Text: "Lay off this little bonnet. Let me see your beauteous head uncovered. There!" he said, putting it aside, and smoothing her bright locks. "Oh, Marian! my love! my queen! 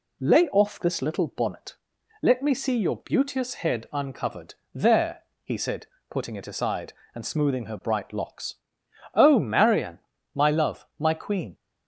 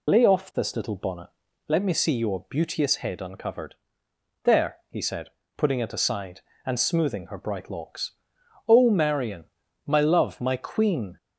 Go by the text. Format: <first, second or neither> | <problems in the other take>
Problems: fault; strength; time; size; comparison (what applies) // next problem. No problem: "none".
first | loses the start of "Lay"; at 0.0 s; 45 ms